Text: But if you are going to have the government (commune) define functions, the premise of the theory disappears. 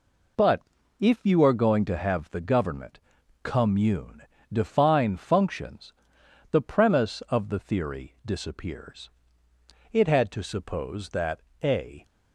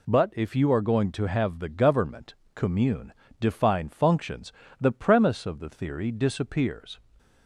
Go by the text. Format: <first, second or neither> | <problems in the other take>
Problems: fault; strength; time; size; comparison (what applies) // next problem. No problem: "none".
second | pauses between "But" and "if"; at 0.6 s; 0.38 s long // goes on to say "It had to suppose that a"; strong; from 9.9 s on; 2.1 s long